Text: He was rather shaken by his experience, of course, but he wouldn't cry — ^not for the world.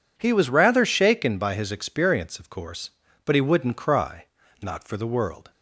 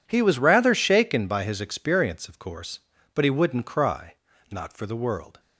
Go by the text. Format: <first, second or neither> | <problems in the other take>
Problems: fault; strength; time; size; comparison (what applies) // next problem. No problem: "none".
first | gets quieter; strong; throughout; 15.5 dB